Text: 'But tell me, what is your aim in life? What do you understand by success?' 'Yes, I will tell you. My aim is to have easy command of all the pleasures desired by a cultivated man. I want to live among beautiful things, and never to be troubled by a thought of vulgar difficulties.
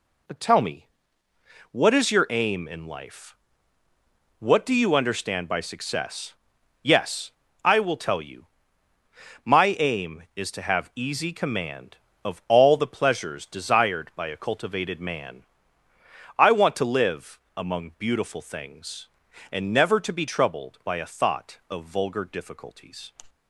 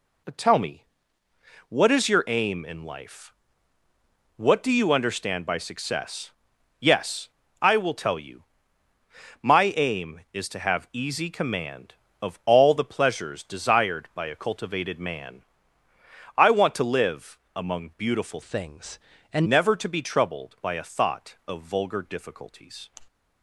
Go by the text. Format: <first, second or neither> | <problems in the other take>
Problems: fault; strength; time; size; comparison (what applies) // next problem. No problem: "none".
first | pauses between "live" and "among"; slight; at 17.3 s; 0.16 s long; slight in the first // changes voice from "things" to "and"; from 18.4 to 19.4 s; 1.0 s long